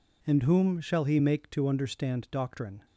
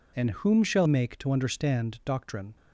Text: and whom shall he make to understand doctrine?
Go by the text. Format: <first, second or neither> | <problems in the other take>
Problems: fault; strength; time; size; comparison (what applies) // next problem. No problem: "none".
first | skips "he"; at 0.8 s